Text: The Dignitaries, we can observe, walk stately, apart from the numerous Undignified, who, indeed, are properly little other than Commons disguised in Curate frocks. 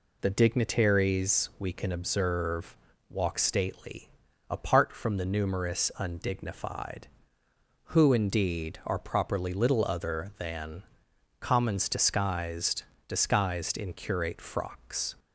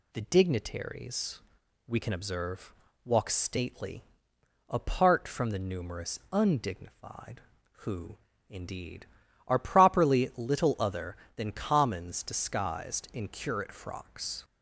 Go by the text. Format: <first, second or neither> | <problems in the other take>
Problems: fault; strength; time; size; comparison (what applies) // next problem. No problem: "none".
second | pauses between "than" and "Commons"; noticeable; at 10.8 s; 0.56 s long // says "disguised" twice; at 13.0 s